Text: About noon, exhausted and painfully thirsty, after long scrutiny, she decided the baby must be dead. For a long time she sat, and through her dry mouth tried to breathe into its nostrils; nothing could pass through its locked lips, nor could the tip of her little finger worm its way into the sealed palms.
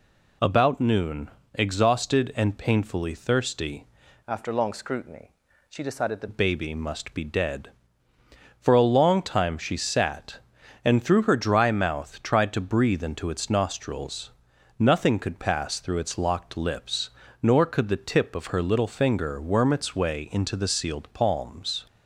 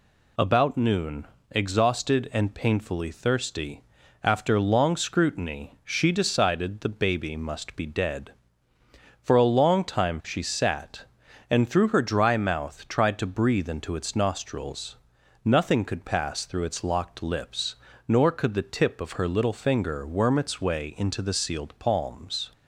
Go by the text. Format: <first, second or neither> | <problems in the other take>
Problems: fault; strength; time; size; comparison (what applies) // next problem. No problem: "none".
second | changes voice from "after" to "the"; from 4.2 to 6.2 s; 2.0 s long